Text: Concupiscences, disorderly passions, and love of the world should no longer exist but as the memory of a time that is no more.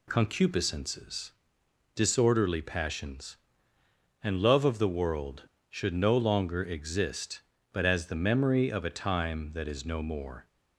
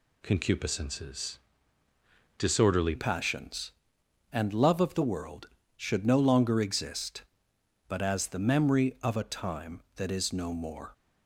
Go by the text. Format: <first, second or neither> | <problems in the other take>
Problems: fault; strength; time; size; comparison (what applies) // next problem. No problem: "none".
first | changes voice at "passions"; from 2.9 s on; 8.0 s long